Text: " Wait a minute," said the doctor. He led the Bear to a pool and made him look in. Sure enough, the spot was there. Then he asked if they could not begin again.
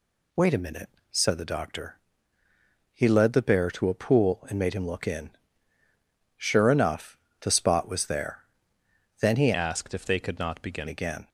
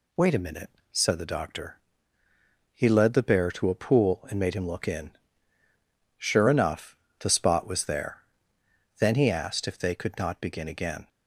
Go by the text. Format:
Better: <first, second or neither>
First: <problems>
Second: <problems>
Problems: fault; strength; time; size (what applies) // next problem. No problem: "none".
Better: second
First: changes voice from "asked" to "begin"; from 9.5 to 10.8 s; 1.3 s long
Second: none